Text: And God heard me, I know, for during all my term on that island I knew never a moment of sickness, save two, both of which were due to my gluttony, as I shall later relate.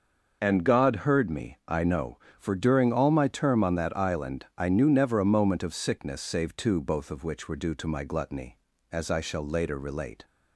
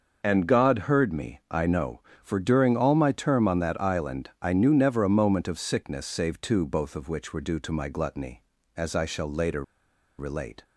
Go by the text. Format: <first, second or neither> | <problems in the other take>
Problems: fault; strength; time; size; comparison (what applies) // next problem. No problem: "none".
first | starts louder than the rest; noticeable; until 1.2 s; 6 dB // pauses between "later" and "relate"; noticeable; at 9.6 s; 0.56 s long